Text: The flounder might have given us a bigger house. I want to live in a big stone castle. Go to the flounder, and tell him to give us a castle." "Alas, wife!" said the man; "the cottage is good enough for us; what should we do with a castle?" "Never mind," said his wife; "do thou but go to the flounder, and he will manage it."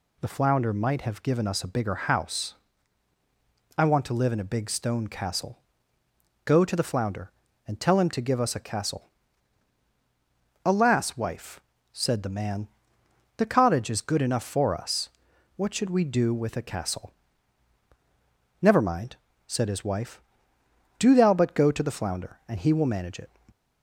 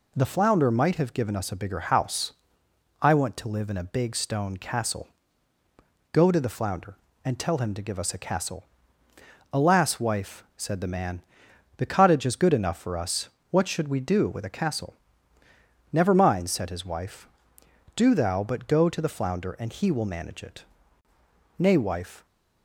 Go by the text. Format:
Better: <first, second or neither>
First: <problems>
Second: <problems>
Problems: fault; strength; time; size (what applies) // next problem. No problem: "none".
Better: first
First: none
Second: goes on to say "Nay wife"; noticeable; from 21.5 s on; 0.66 s long